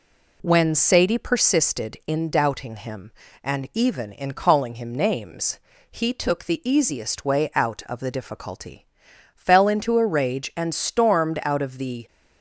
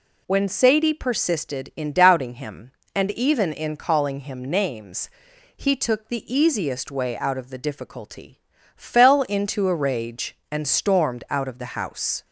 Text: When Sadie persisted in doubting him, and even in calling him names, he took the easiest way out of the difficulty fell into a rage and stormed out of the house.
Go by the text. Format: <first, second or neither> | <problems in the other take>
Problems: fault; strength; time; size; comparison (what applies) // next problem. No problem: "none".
second | pauses between "difficulty" and "fell"; noticeable; at 8.8 s; 0.48 s long; slight in the second // stops before "house"; at 12.0 s